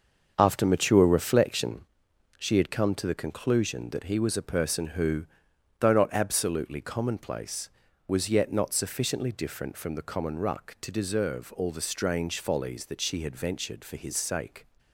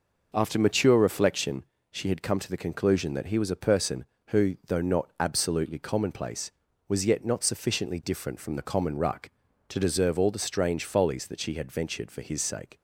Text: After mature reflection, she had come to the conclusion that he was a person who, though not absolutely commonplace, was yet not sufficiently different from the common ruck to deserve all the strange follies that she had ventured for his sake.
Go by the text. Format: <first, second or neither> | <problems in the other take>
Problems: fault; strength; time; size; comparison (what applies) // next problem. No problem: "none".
second | gets quieter; strong; throughout; 7.5 dB